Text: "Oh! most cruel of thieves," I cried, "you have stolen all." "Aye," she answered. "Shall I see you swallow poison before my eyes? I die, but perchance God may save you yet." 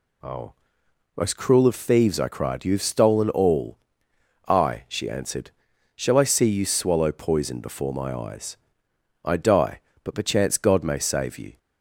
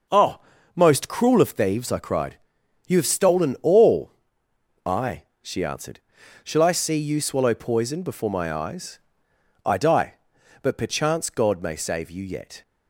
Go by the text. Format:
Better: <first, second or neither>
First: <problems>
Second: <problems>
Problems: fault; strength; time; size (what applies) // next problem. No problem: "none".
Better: second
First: stops before "yet"; at 11.5 s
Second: none